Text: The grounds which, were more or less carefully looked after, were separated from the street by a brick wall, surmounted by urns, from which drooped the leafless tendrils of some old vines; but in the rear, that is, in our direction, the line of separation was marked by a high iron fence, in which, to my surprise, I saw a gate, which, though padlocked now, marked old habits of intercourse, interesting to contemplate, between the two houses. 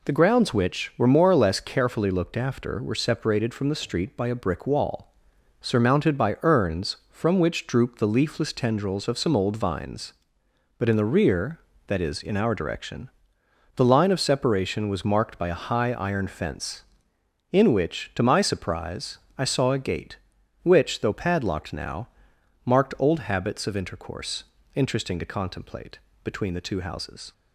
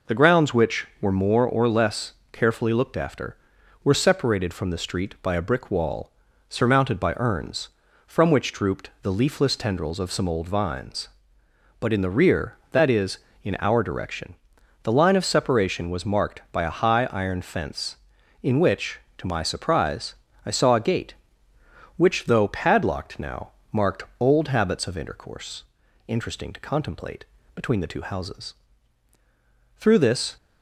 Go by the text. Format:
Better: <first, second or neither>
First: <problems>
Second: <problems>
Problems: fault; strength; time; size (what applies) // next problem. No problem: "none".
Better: first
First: none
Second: pauses between "less" and "carefully"; slight; at 2.1 s; 0.20 s long // pauses between "marked" and "old"; slight; at 24.0 s; 0.16 s long // goes on to say "Through this"; from 29.7 s on; 0.58 s long